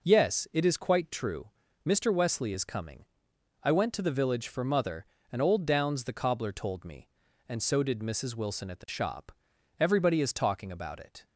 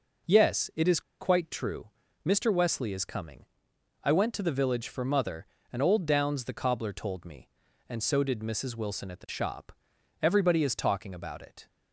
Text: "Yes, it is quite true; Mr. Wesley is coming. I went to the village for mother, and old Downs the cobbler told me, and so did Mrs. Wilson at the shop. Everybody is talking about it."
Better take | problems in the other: first | pauses between "is" and "quite"; slight; at 0.9 s; 0.19 s long

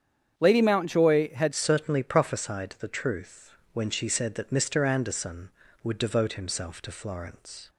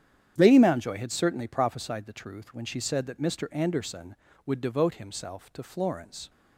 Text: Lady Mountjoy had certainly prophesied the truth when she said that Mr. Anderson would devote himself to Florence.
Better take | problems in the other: second | starts louder than the rest; strong; until 1.3 s; 8.5 dB; strong in the second // changes voice at "certainly"; from 1.5 s on; 6.1 s long // pauses between "truth" and "when"; slight; at 3.5 s; 0.22 s long

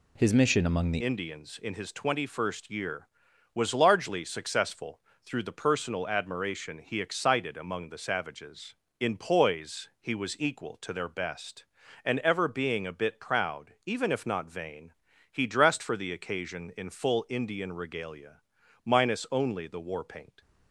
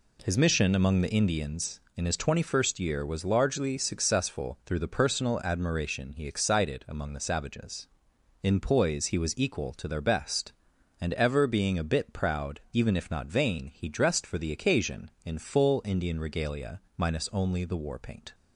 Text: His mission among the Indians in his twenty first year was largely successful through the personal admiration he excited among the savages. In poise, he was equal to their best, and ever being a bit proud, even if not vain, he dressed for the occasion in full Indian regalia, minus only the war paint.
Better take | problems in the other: second | changes voice at "Indians"; from 1.0 s on; 19.4 s long // pauses between "successful" and "through"; slight; at 4.9 s; 0.24 s long

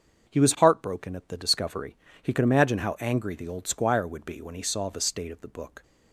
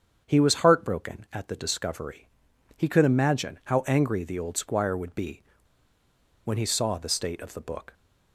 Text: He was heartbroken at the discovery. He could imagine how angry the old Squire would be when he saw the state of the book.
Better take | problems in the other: first | starts louder than the rest; strong; until 1.2 s; 7.5 dB; also in the first // pauses between "be" and "when"; at 5.4 s; 1.0 s long

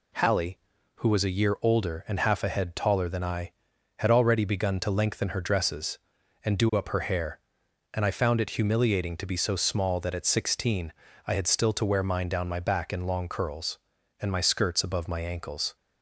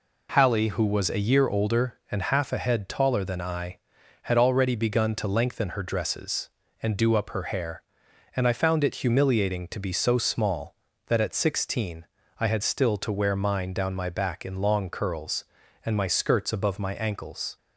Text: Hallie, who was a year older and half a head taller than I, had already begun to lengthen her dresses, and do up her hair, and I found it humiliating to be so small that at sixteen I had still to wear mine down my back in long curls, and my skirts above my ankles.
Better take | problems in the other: neither | pauses between "sixteen" and "I"; slight; the same in both

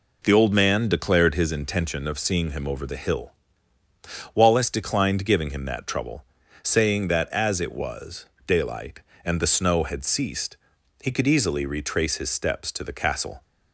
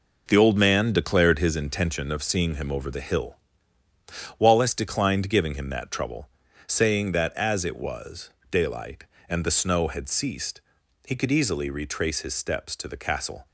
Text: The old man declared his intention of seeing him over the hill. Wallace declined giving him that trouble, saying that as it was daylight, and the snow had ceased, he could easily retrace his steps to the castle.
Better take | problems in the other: first | gets quieter; strong; throughout; 8 dB // pauses between "was" and "daylight"; slight; at 8.2 s; 0.22 s long; slight in the first

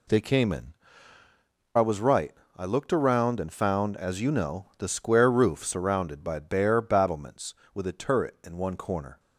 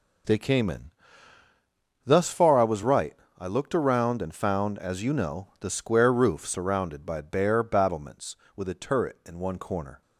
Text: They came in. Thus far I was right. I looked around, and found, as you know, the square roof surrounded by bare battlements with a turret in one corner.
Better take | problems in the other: second | skips "Thus far"; at 1.2 s

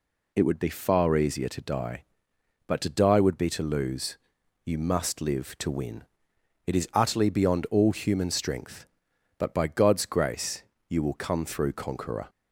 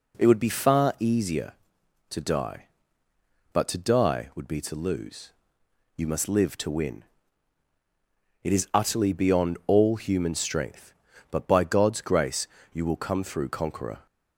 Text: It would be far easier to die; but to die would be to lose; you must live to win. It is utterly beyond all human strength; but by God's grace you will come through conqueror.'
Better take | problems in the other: neither | pauses between "grace" and "you"; slight; the same in both

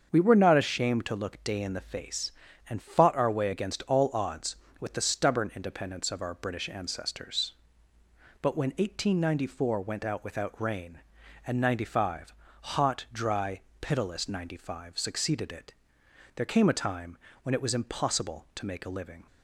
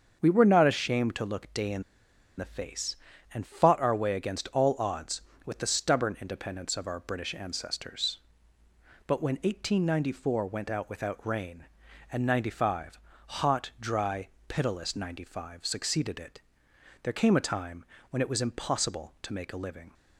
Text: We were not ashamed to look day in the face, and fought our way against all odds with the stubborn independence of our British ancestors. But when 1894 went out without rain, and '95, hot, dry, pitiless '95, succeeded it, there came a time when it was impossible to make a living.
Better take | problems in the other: first | starts louder than the rest; until 1.2 s; 7 dB; also in the first // pauses between "in" and "the"; noticeable; at 1.8 s; 0.55 s long // pauses between "time" and "when"; slight; at 17.8 s; 0.24 s long; slight in the first

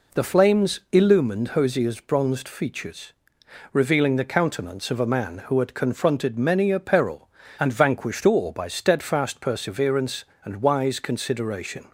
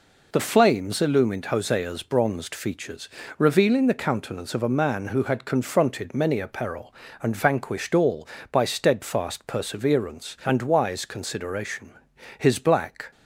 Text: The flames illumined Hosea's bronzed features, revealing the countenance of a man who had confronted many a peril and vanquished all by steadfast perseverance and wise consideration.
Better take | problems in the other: first | goes on to say "His black"; noticeable; from 12.3 s on; 0.72 s long

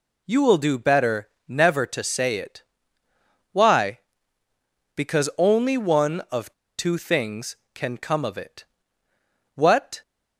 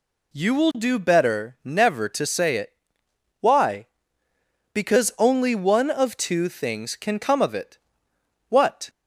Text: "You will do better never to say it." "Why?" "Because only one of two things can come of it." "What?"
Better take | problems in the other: second | pauses between "better" and "never"; slight; at 1.2 s; 0.18 s long // pauses between "of" and "two"; slight; at 6.5 s; 0.26 s long

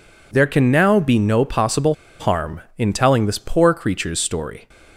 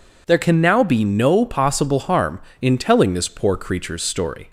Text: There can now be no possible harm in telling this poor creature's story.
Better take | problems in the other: second | pauses between "possible" and "harm"; slight; at 1.9 s; 0.27 s long

